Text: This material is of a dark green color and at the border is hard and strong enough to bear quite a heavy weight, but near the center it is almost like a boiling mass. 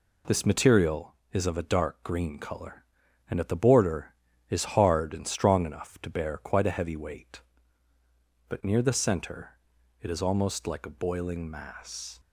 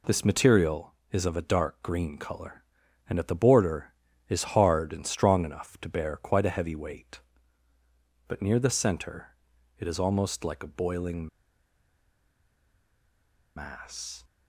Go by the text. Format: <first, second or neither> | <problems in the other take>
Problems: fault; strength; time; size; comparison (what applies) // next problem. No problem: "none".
first | pauses between "center" and "it"; noticeable; at 9.2 s; 0.50 s long; noticeable in the first // pauses between "boiling" and "mass"; strong; at 11.2 s; 2.2 s long